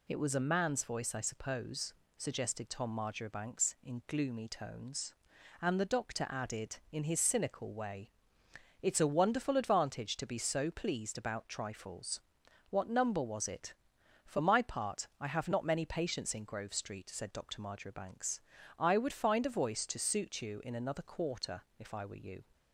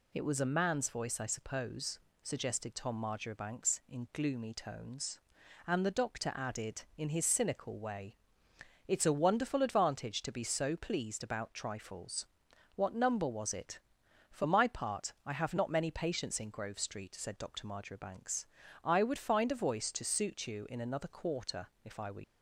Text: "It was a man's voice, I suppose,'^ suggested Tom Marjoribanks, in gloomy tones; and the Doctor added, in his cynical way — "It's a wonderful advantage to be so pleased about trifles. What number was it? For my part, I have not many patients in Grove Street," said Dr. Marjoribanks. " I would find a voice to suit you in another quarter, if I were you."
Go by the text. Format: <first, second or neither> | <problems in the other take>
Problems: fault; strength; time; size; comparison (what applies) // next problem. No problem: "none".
first | stops before "you"; at 22.2 s